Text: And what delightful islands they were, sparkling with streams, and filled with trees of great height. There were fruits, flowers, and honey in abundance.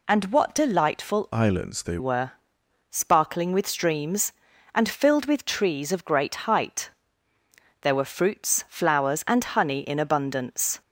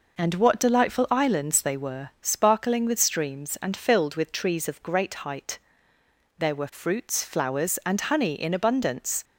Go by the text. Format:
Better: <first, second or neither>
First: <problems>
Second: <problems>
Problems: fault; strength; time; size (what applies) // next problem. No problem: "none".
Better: second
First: changes voice from "islands" to "they"; from 1.3 to 1.9 s; 0.6 s long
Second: none